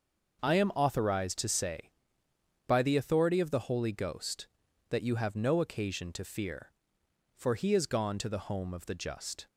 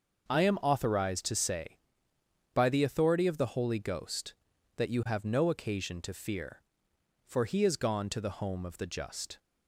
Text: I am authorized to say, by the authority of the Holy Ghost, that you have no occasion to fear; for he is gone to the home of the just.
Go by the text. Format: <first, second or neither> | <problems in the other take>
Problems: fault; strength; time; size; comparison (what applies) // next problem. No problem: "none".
neither | none